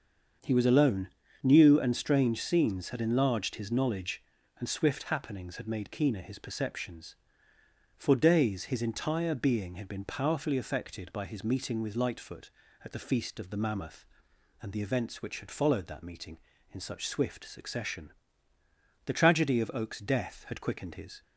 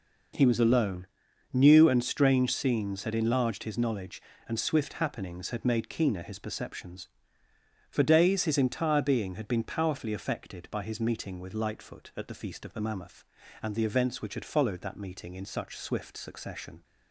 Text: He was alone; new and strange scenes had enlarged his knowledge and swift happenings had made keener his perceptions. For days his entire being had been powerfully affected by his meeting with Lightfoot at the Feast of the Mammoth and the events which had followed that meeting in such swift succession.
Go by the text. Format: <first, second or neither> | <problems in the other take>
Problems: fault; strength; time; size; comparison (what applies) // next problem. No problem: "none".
second | starts louder than the rest; until 1.7 s; 7 dB // goes on to say "The tragedy of Oak's death had quickened his"; strong; from 19.0 s on; 2.1 s long